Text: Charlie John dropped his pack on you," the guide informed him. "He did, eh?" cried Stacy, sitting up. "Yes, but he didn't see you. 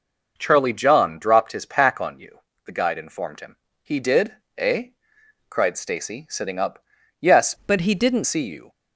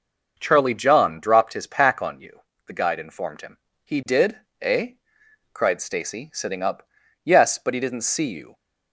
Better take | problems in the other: second | changes voice from "but" to "didn't"; from 7.6 to 8.2 s; 0.6 s long

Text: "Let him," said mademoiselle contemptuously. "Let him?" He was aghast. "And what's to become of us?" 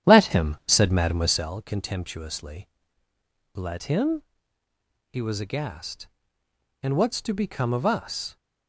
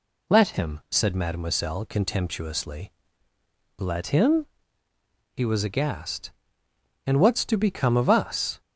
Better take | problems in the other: second | starts louder than the rest; strong; until 1.5 s; 10 dB

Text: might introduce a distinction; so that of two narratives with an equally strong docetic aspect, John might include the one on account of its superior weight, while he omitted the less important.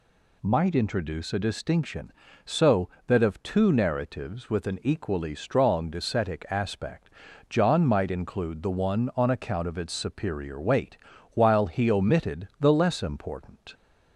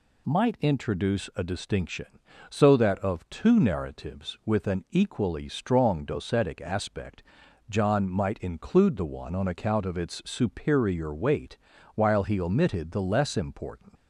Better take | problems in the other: first | leaves "important" unfinished; at 13.9 s; 100 ms

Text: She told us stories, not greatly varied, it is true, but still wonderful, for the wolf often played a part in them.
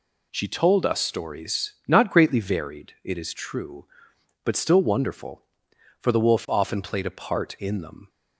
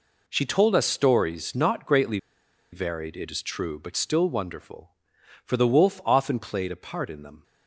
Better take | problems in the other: first | pauses between "greatly" and "varied"; noticeable; at 2.1 s; 0.54 s long

